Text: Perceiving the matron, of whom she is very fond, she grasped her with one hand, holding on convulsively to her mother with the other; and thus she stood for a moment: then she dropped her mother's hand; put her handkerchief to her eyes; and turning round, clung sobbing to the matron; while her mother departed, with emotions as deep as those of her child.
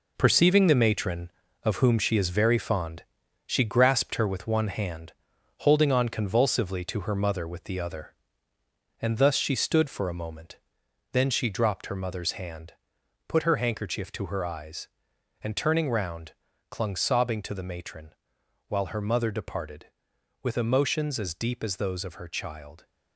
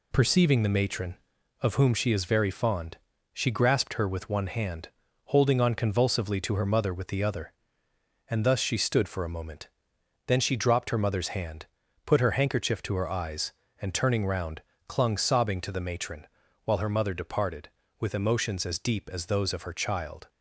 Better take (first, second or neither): second